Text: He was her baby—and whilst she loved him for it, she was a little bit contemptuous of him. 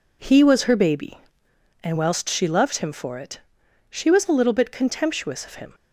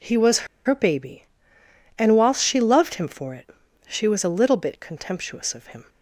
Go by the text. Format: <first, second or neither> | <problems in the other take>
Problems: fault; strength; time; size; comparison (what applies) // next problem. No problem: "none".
first | pauses between "was" and "her"; slight; at 0.4 s; 0.20 s long